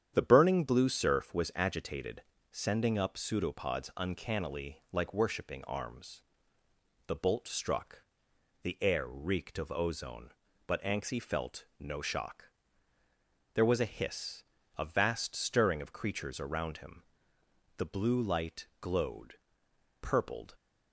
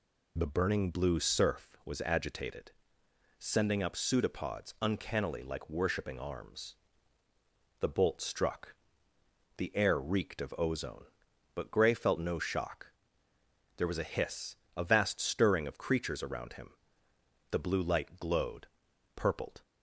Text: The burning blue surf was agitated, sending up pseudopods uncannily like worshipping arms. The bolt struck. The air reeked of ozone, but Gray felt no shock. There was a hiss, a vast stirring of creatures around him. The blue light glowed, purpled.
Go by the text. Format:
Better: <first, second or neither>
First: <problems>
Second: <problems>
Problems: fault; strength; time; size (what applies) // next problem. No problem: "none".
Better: second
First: starts louder than the rest; strong; until 1.1 s; 9 dB // says "Anxie" for "Gray"; at 10.8 s // pauses between "felt" and "no"; slight; at 11.6 s; 0.16 s long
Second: none